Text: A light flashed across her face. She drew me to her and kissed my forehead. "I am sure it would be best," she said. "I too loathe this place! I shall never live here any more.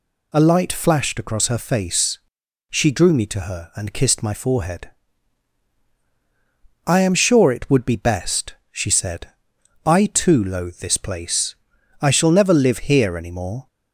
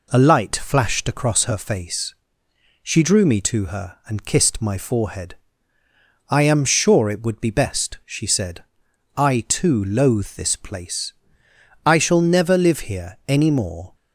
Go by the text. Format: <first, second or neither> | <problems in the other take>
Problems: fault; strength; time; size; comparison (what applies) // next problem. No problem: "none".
neither | none